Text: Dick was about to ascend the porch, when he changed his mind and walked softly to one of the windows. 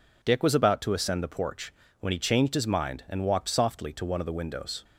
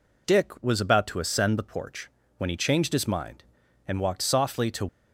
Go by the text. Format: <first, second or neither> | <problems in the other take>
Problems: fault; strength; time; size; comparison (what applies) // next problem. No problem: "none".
first | stops before "one of the windows"; at 4.8 s